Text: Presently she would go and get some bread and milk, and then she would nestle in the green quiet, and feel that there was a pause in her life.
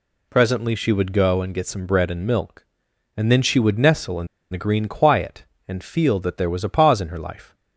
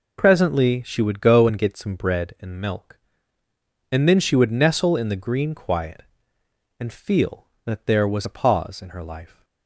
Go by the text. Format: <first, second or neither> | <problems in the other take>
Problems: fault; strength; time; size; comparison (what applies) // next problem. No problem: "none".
second | pauses between "in" and "the"; slight; at 4.2 s; 0.24 s long